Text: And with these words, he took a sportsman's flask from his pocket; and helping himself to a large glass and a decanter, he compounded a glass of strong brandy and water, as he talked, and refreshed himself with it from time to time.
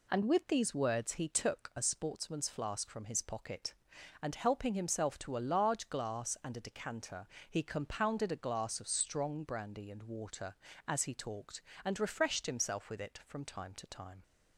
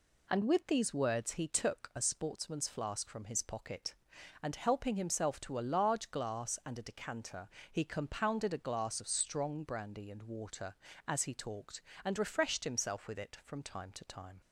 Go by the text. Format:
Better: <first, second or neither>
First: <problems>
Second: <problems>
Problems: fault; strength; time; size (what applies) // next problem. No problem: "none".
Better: neither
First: none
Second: none